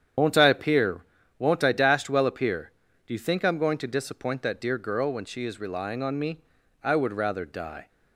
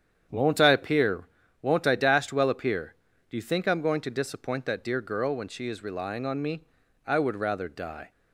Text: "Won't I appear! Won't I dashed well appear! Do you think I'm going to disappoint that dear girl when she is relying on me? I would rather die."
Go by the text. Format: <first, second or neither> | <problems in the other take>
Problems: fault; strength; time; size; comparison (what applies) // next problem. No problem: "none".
second | loses the start of "Won't"; at 0.1 s; 105 ms // starts louder than the rest; strong; until 1.5 s; 8.5 dB; strong in the second